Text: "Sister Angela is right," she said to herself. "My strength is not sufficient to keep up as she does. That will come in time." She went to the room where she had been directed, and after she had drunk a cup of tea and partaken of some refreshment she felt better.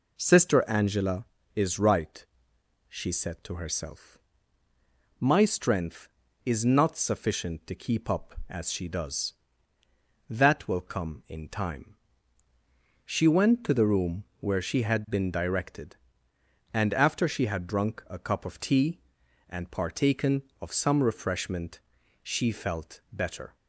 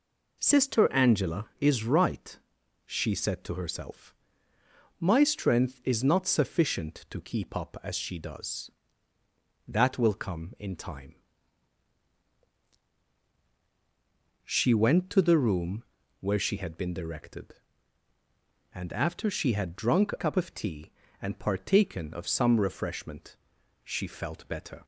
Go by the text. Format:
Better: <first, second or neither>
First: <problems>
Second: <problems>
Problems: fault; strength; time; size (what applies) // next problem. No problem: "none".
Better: first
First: pauses between "room" and "where"; slight; at 14.2 s; 0.16 s long // pauses between "refreshment" and "she"; at 21.7 s; 0.44 s long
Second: pauses between "room" and "where"; slight; at 15.8 s; 0.36 s long // changes voice from "a" to "cup"; from 20.1 to 20.3 s; 0.2 s long // pauses between "refreshment" and "she"; noticeable; at 23.3 s; 0.46 s long